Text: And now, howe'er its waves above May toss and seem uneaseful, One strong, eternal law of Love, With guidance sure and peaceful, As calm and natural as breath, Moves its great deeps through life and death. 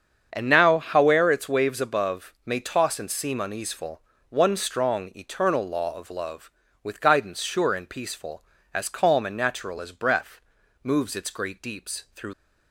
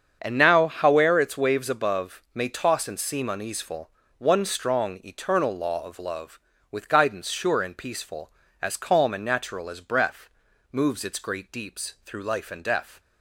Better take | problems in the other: second | starts louder than the rest; strong; until 1.3 s; 7.5 dB; strong in the second // stops before "life and death"; at 12.3 s

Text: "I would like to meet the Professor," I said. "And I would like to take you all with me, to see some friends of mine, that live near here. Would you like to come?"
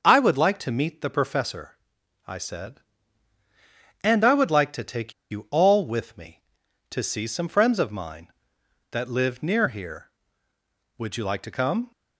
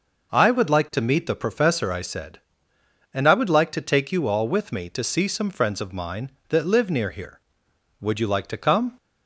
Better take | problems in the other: second | starts louder than the rest; until 1.0 s; 6.5 dB // pauses between "take" and "you"; slight; at 5.1 s; 0.17 s long

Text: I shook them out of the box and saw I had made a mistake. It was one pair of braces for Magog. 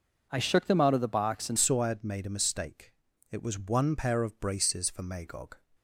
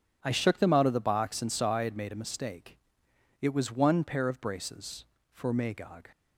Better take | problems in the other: second | changes voice at "saw"; from 1.5 s on; 4.0 s long

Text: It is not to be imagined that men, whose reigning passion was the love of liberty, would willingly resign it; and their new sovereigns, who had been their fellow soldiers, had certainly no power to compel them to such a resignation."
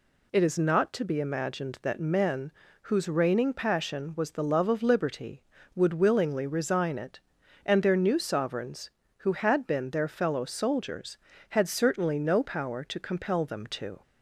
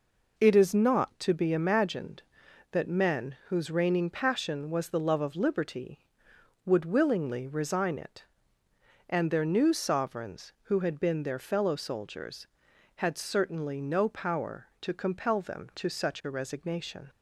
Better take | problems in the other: second | stops before "such a resignation"; at 14.0 s

